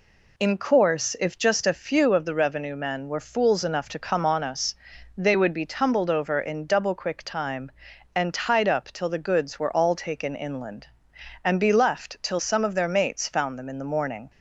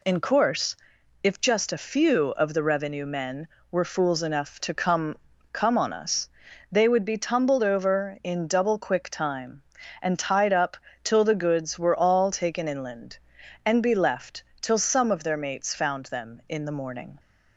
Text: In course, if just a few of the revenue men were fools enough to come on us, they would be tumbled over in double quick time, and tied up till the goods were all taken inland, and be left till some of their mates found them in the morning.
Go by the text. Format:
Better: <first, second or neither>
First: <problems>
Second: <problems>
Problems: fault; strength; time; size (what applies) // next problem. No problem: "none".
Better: first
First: none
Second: says "come" twice; at 5.5 s // pauses between "up" and "till"; slight; at 10.7 s; 0.26 s long // pauses between "left" and "till"; slight; at 14.4 s; 0.20 s long